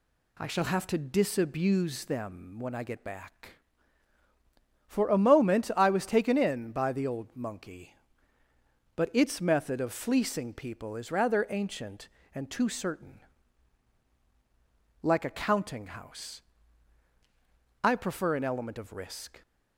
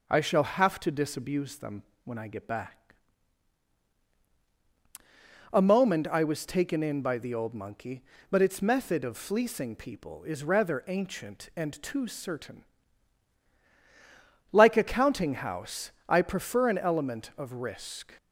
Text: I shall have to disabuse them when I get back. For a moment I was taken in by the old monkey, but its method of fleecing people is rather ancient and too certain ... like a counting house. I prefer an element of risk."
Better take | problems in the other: first | pauses between "them" and "when"; slight; at 1.8 s; 0.22 s long // skips "For"; at 4.1 s

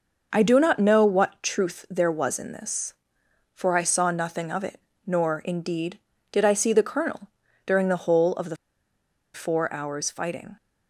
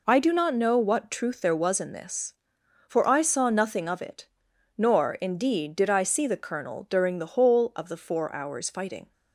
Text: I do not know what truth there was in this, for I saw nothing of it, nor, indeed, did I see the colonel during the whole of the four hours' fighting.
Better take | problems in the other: second | pauses between "colonel" and "during"; slight; at 7.2 s; 0.36 s long // pauses between "the" and "four"; noticeable; at 8.5 s; 0.77 s long

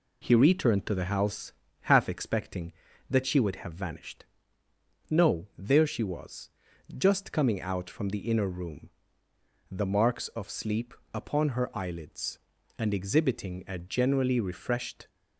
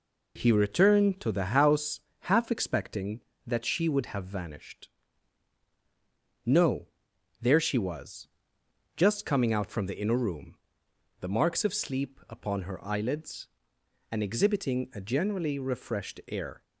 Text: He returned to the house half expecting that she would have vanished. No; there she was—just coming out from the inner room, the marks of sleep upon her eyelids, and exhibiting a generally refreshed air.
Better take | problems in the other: second | pauses between "house" and "half"; at 1.5 s; 0.40 s long; slight in the second // pauses between "sleep" and "upon"; slight; at 10.9 s; 0.18 s long // stops before "air"; at 15.0 s

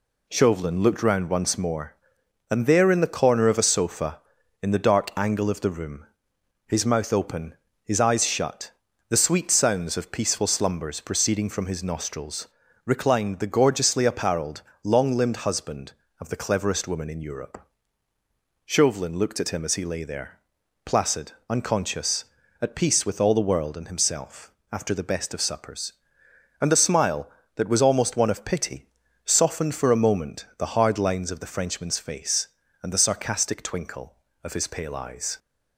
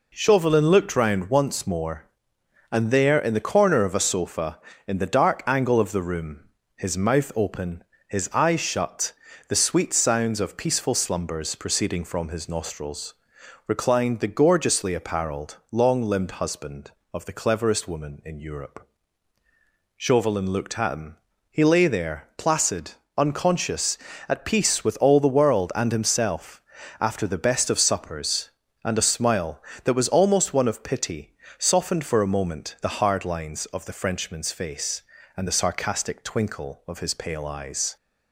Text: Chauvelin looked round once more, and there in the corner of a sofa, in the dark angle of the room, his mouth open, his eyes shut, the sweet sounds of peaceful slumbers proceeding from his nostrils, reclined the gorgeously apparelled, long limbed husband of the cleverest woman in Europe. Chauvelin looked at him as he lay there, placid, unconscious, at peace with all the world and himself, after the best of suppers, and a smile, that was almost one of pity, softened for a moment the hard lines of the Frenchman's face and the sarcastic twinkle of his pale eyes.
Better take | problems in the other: first | skips "as"; at 21.3 s

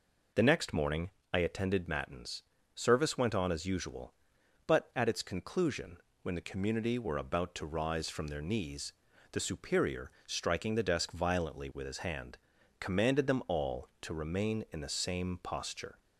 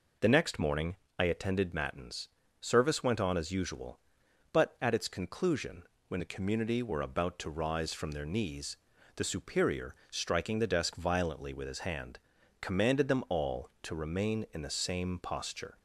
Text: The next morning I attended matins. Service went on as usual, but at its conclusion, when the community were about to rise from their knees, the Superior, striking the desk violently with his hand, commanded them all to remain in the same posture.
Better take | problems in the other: neither | pauses between "morning" and "I"; slight; the same in both

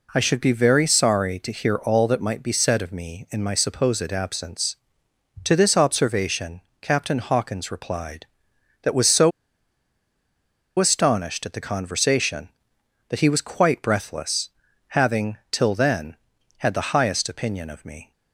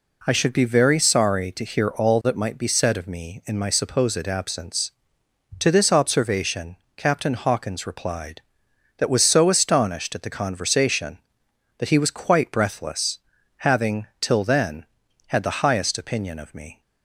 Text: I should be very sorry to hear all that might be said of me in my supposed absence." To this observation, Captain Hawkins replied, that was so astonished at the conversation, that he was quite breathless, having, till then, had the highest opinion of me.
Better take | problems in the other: second | pauses between "so" and "astonished"; strong; at 9.3 s; 1.4 s long

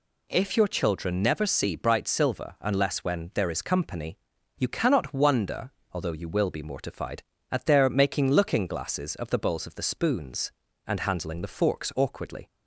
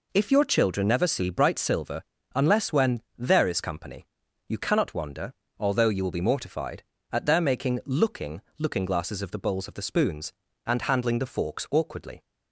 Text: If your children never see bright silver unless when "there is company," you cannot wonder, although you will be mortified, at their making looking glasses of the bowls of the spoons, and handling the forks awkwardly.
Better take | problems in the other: first | pauses between "silver" and "unless"; slight; at 2.0 s; 0.32 s long // says "looking" twice; at 8.5 s

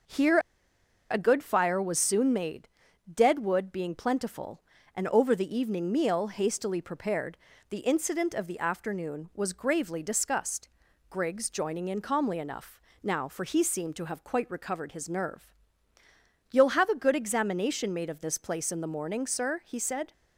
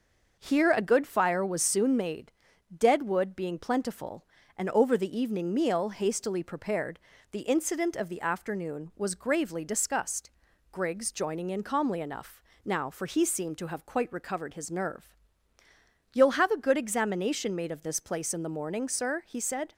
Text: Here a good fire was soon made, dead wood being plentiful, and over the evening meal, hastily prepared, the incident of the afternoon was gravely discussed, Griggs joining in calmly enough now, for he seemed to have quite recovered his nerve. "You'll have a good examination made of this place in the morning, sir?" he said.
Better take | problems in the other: second | starts louder than the rest; noticeable; until 1.7 s; 6 dB; noticeable in the second // pauses between "Here" and "a"; noticeable; at 0.3 s; 0.71 s long // pauses between "enough" and "now"; slight; at 12.8 s; 0.26 s long; slight in the second

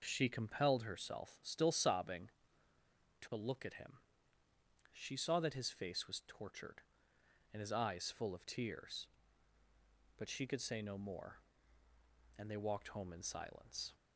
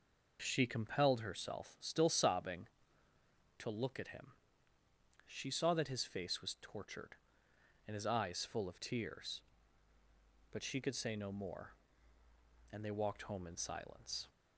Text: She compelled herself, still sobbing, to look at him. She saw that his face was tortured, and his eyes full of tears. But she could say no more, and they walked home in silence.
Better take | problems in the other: neither | none

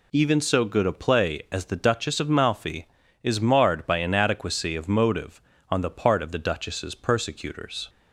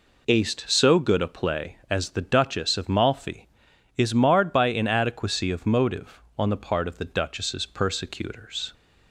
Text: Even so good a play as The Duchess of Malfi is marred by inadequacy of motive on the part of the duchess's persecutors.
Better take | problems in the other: first | says "Aced" for "Even"; at 0.2 s

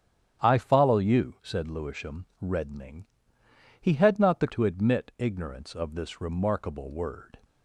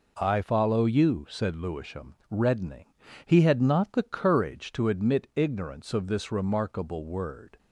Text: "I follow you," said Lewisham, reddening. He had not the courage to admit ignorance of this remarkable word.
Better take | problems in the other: second | starts louder than the rest; strong; until 1.4 s; 9.5 dB // skips "courage"; at 4.4 s

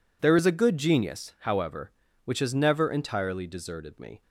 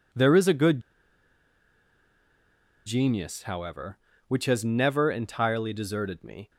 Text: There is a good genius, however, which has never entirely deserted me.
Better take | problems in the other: first | pauses between "good" and "genius"; strong; at 0.8 s; 2.0 s long

